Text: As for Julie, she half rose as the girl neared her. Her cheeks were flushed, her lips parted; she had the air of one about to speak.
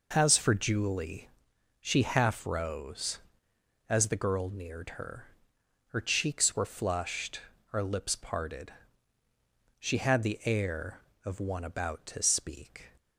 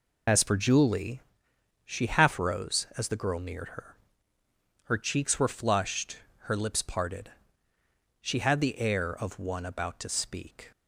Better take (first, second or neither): first